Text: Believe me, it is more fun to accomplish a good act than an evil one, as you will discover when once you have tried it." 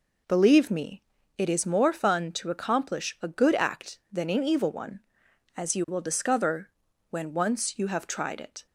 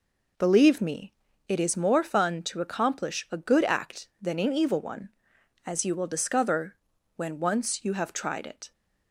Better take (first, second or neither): neither